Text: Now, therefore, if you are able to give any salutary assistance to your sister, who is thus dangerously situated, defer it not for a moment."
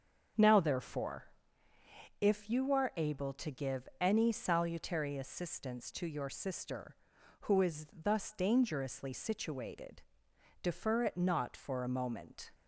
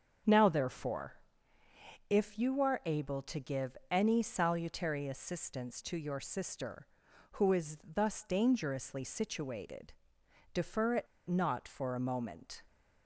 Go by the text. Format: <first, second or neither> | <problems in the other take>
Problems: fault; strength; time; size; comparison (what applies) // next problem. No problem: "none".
first | starts louder than the rest; strong; until 2.1 s; 7 dB; strong in the first // pauses between "it" and "not"; slight; at 11.0 s; 0.21 s long